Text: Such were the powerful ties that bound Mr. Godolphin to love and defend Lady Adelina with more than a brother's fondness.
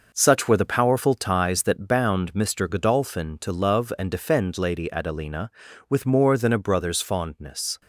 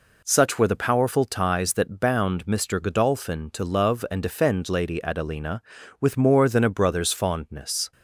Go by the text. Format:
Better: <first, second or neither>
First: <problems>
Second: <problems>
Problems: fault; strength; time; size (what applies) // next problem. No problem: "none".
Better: second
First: gets quieter; strong; throughout; 7.5 dB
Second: none